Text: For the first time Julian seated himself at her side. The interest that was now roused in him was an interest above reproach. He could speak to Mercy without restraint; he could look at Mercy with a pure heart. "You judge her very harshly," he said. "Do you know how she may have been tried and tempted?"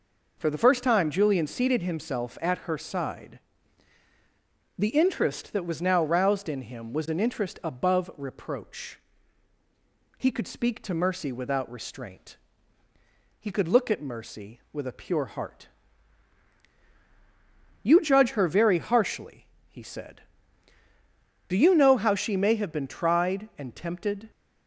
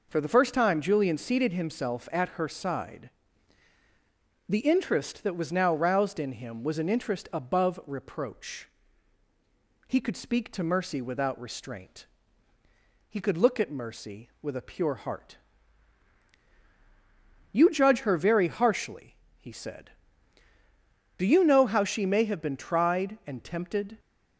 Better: neither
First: none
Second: none

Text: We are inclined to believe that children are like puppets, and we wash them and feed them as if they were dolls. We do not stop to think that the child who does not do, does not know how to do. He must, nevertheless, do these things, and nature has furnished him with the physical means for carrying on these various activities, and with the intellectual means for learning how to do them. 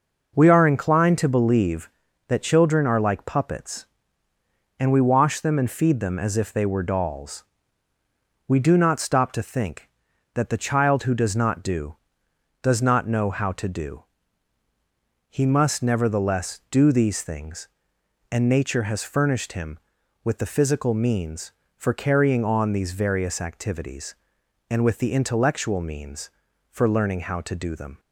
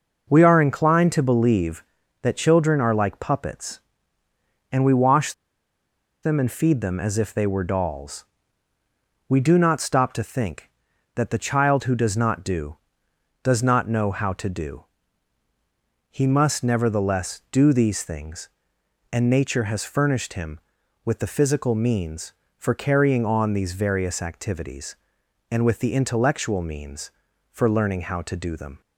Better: first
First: none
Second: pauses between "wash" and "them"; noticeable; at 5.3 s; 0.90 s long

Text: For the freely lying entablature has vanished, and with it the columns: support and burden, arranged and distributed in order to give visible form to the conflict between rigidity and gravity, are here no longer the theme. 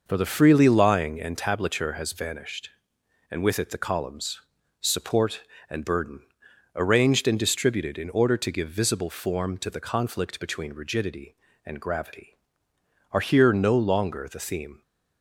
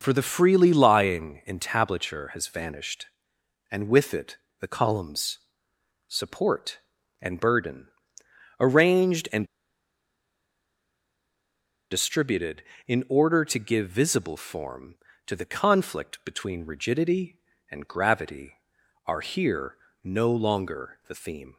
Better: first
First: none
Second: pauses between "it" and "the"; slight; at 4.3 s; 0.22 s long // pauses between "and" and "distributed"; strong; at 9.4 s; 2.4 s long // pauses between "here" and "no"; slight; at 19.7 s; 0.30 s long

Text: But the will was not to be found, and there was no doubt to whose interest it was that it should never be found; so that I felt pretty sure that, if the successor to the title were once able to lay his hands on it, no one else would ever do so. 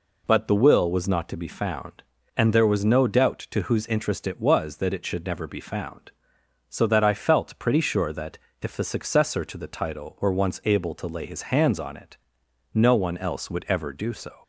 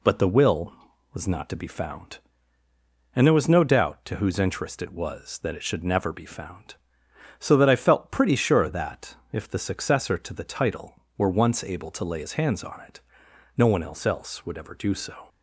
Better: first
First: none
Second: says "else" twice; at 14.0 s

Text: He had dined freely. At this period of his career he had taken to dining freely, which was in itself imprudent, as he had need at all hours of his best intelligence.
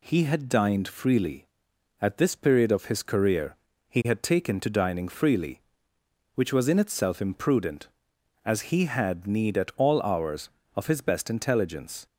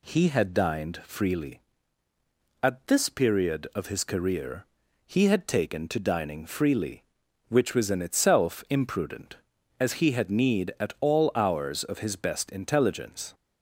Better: neither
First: pauses between "career" and "he"; slight; at 3.5 s; 0.32 s long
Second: pauses between "career" and "he"; at 4.6 s; 0.40 s long

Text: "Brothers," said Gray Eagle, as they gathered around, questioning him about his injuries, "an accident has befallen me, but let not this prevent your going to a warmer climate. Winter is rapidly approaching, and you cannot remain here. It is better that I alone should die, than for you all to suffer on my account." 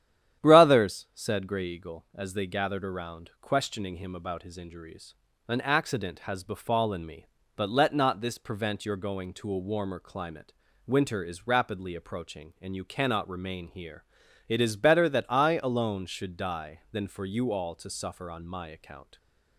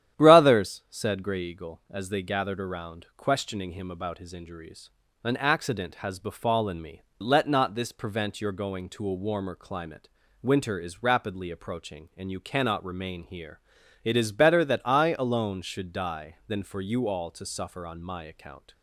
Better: first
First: starts louder than the rest; strong; until 1.4 s; 10.5 dB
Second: starts louder than the rest; strong; until 1.2 s; 10.5 dB // skips "but"; at 7.1 s

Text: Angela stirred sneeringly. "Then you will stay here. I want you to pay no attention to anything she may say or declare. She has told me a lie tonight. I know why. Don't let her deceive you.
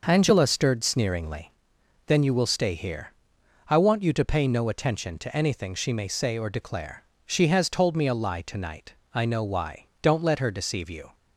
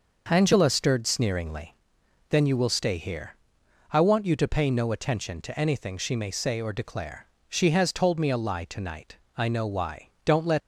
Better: first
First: none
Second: stops before "her deceive you"; at 10.5 s

